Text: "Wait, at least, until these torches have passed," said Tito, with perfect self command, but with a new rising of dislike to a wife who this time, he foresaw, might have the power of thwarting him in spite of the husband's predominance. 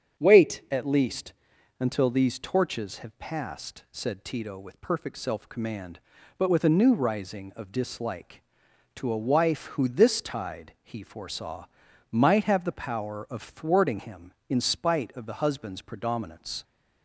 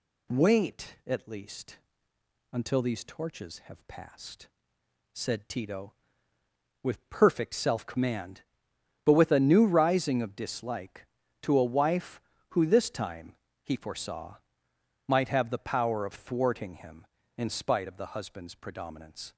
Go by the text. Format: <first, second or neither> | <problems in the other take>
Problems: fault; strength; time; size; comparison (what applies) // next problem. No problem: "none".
second | starts louder than the rest; strong; until 1.2 s; 7.5 dB // says "tide" for "time"; at 10.2 s